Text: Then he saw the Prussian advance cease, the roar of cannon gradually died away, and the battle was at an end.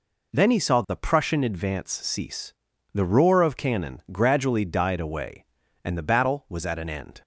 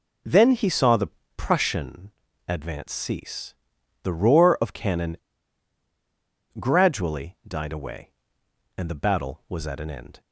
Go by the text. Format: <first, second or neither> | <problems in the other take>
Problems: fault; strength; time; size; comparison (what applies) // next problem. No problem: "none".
first | pauses between "the" and "Prussian"; slight; at 1.0 s; 0.26 s long // pauses between "Prussian" and "advance"; slight; at 2.1 s; 0.36 s long // pauses between "cannon" and "gradually"; strong; at 5.1 s; 1.4 s long